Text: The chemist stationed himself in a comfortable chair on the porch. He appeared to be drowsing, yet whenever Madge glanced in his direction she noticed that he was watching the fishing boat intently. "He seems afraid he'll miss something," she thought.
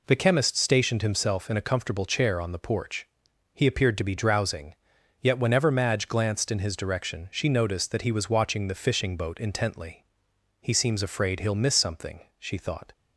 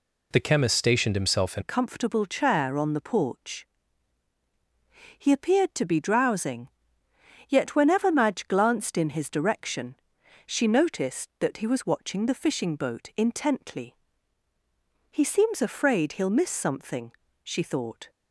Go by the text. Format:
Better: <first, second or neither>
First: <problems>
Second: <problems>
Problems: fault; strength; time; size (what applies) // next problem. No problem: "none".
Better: first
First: none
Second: changes voice at "a"; from 1.6 s on; 16.4 s long // pauses between "direction" and "she"; noticeable; at 9.9 s; 0.50 s long